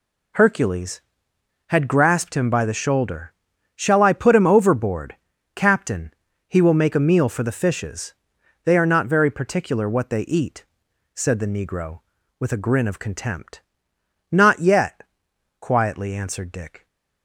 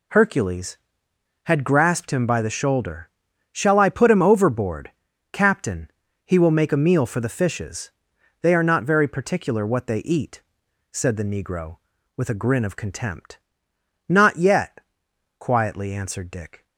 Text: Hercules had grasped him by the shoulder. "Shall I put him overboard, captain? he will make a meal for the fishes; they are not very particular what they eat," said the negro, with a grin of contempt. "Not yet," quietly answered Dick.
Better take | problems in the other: neither | none

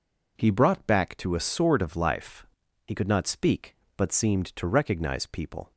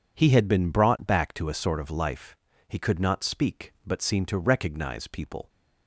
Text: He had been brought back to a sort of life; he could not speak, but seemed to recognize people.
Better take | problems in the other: second | skips "had been"; at 0.4 s

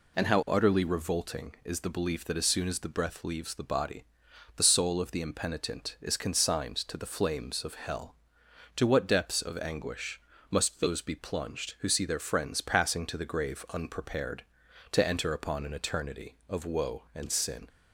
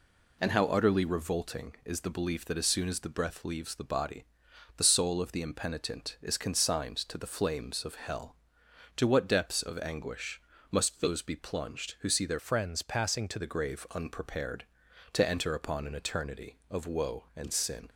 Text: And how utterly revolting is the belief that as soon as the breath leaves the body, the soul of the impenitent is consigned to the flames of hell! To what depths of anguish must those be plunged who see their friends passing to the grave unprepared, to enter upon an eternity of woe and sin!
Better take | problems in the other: first | pauses between "anguish" and "must"; slight; at 10.4 s; 0.30 s long; slight in the first // changes voice from "friends" to "to"; from 12.3 to 13.3 s; 1.0 s long

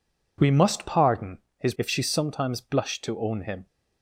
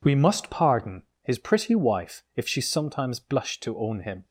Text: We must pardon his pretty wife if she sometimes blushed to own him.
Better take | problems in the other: second | pauses between "pardon" and "his"; slight; at 1.3 s; 0.18 s long; slight in the second // skips "pretty wife"; at 1.7 s

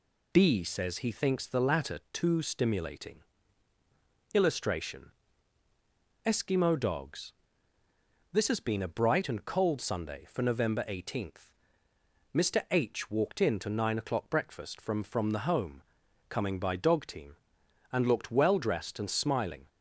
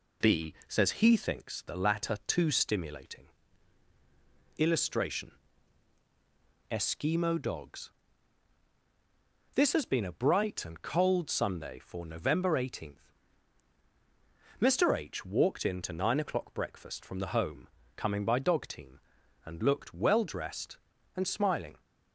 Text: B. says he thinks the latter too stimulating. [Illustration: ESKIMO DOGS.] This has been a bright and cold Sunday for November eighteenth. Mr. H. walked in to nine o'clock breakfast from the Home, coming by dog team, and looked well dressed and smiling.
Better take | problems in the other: second | says "from" twice; at 15.0 s

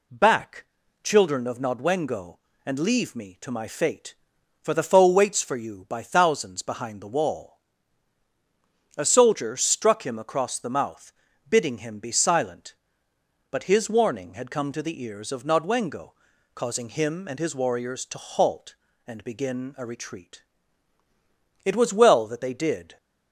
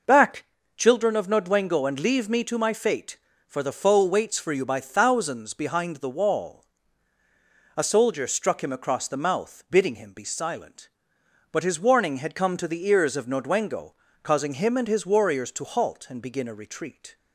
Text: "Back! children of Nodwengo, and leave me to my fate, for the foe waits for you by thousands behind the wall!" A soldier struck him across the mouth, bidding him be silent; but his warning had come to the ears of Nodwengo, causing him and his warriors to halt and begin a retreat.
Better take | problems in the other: second | goes on to say "It was well that they did"; from 21.6 s on; 1.3 s long

